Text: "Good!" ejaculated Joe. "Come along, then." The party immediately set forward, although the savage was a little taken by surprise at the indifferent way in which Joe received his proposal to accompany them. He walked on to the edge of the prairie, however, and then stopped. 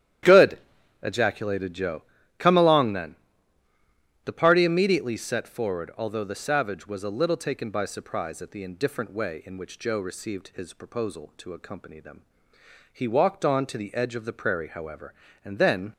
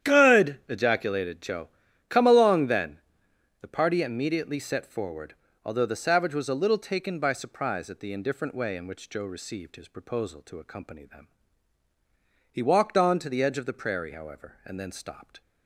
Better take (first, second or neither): second